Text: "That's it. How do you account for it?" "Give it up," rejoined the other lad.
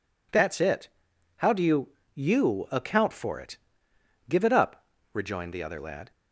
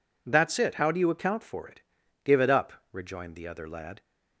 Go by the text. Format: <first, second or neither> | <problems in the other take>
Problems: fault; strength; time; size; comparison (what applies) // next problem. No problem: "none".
second | says "you" twice; at 2.1 s